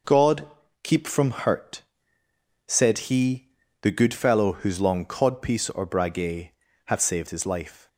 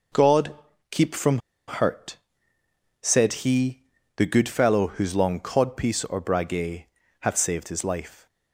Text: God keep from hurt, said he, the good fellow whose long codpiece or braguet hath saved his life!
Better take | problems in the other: first | pauses between "God" and "keep"; at 0.5 s; 0.38 s long; also in the first // pauses between "from" and "hurt"; slight; at 1.3 s; 0.28 s long // pauses between "braguet" and "hath"; slight; at 6.8 s; 0.34 s long; slight in the first

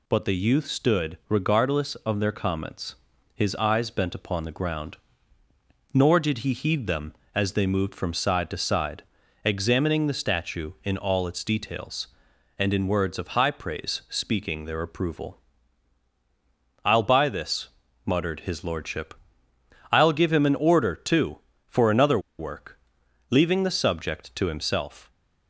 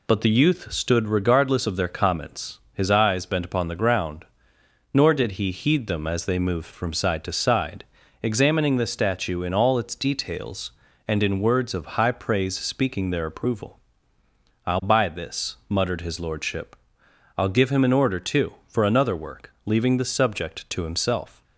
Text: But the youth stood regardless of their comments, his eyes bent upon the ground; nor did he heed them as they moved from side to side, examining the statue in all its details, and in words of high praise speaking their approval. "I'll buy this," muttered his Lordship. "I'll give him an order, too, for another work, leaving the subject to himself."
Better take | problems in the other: second | pauses between "another" and "work"; slight; at 22.1 s; 0.19 s long

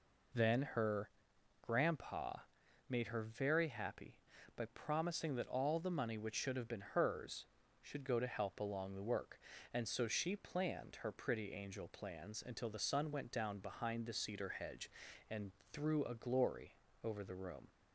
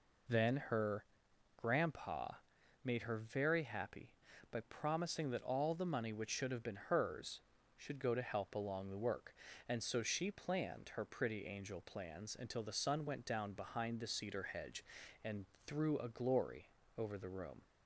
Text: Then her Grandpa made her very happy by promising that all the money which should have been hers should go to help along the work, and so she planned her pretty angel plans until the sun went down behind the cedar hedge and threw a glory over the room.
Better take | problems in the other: neither | pauses between "her" and "Grandpa"; noticeable; the same in both // pauses between "Grandpa" and "made"; noticeable; the same in both // pauses between "and" and "threw"; slight; the same in both // pauses between "glory" and "over"; slight; the same in both

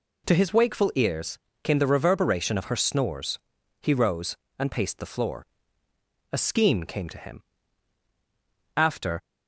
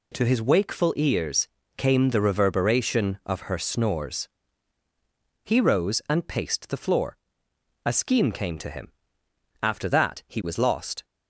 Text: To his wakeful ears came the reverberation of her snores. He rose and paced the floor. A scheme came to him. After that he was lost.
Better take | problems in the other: second | pauses between "ears" and "came"; slight; at 1.3 s; 0.26 s long; slight in the second // stops before "that he was lost"; at 9.2 s

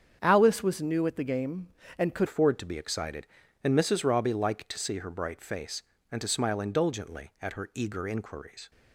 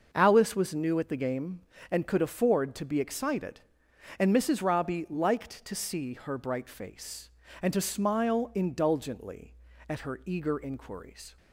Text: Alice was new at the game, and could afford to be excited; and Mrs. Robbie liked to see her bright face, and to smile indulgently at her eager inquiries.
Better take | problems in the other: second | starts louder than the rest; strong; until 1.2 s; 7.5 dB; also in the second // changes voice at "afford"; from 2.2 s on; 6.5 s long

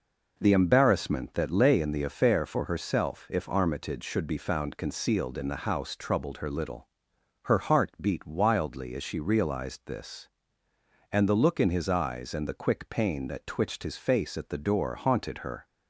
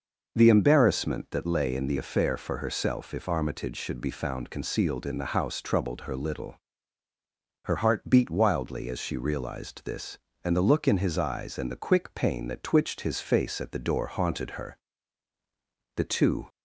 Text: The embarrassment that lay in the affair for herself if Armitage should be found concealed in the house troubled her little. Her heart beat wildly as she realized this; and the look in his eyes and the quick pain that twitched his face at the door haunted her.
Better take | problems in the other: first | goes on to say "The two"; from 15.9 s on; 0.54 s long

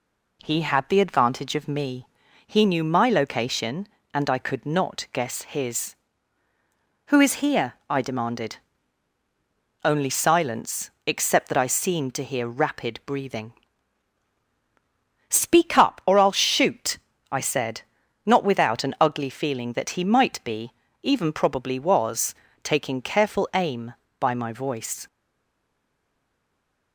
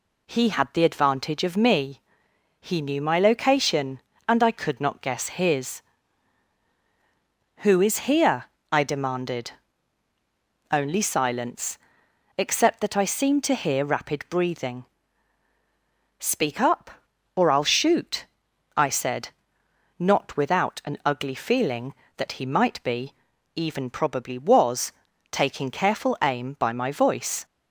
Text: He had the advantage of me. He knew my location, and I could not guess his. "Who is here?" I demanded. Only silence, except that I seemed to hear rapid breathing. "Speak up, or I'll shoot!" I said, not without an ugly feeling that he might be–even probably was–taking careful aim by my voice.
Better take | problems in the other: second | stays silent after the last word; noticeable; from 25.0 s on; 1.9 s long

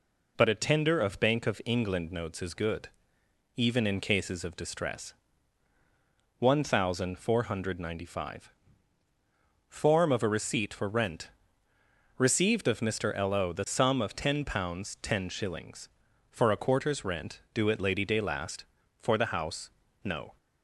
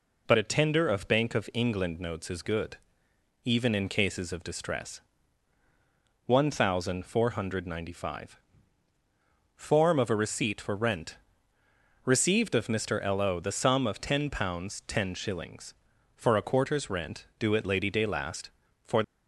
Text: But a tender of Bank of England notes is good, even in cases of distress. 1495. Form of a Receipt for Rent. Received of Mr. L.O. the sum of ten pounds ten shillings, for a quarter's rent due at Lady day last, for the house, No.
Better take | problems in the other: first | stops before "the house No"; at 19.0 s

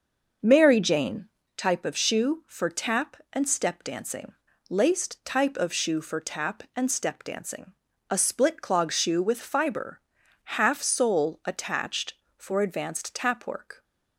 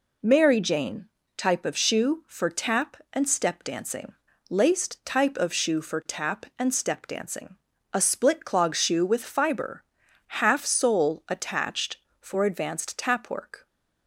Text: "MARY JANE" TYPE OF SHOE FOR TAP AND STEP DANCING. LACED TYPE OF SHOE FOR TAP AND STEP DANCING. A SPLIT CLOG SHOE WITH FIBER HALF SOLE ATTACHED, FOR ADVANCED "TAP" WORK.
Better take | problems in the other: second | starts louder than the rest; noticeable; until 1.5 s; 6 dB // pauses between "JANE" and "TYPE"; slight; at 1.2 s; 0.28 s long; slight in the second // pauses between "FIBER" and "HALF"; at 9.9 s; 0.44 s long; also in the second

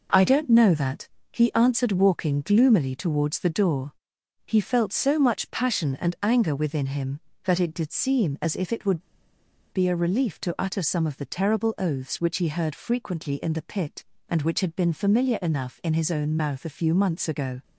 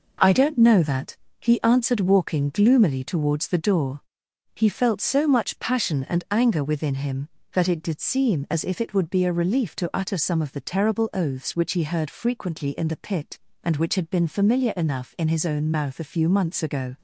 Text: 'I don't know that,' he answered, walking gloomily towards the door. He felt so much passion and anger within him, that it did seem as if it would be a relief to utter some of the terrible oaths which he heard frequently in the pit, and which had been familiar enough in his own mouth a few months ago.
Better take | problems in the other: second | pauses between "would" and "be"; noticeable; at 9.0 s; 0.71 s long

